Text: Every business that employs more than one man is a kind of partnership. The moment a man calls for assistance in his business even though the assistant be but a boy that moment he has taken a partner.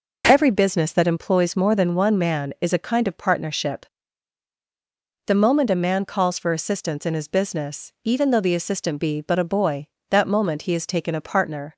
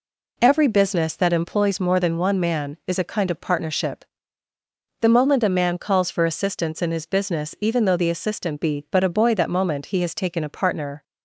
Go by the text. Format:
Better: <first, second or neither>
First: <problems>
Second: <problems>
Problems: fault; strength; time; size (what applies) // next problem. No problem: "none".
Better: neither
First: none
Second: none